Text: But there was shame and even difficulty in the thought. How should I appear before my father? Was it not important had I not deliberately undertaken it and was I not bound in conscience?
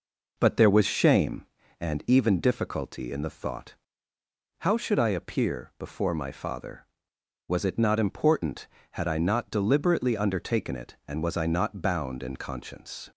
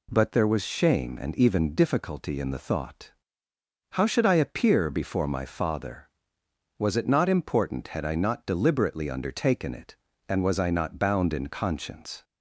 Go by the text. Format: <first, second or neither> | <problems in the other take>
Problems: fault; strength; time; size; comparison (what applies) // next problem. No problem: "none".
second | starts louder than the rest; noticeable; until 1.5 s; 5 dB